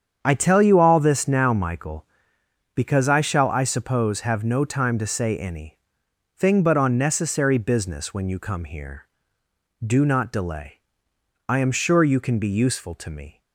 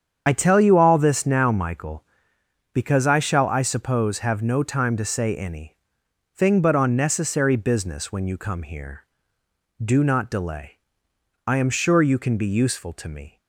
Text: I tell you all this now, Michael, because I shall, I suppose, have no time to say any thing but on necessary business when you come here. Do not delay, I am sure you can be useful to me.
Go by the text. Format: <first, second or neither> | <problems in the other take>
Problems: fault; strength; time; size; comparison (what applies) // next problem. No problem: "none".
first | loses the start of "I"; at 0.2 s; 50 ms // starts louder than the rest; strong; until 1.2 s; 8 dB; strong in the first // pauses between "any" and "thing"; noticeable; at 5.7 s; 0.58 s long; noticeable in the first